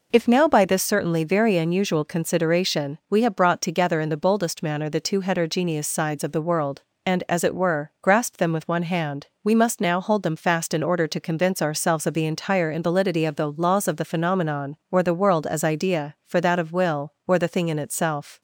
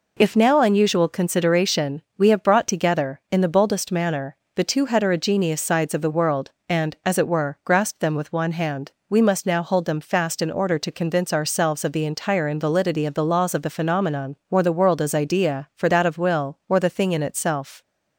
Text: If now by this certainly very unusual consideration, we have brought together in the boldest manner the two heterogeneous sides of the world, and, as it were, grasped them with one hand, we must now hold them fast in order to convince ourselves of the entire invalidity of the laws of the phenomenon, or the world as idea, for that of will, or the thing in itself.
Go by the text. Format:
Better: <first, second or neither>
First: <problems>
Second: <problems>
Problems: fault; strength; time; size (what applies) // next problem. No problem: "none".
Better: first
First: none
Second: skips "by this certainly very"; at 0.6 s // pauses between "manner" and "the"; slight; at 4.3 s; 0.20 s long